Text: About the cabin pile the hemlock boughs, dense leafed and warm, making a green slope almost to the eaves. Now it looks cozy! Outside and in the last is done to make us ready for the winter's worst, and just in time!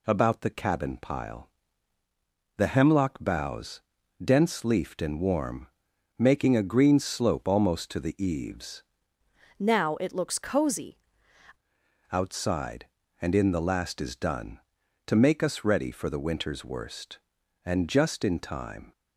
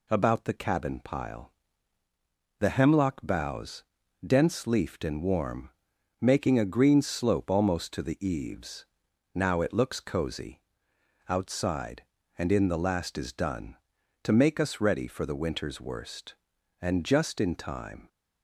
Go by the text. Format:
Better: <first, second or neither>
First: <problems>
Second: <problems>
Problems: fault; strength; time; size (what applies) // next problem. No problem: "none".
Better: second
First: pauses between "pile" and "the"; at 1.4 s; 1.1 s long // changes voice from "Now" to "cozy"; from 9.5 to 10.9 s; 1.4 s long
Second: pauses between "pile" and "the"; at 1.5 s; 1.1 s long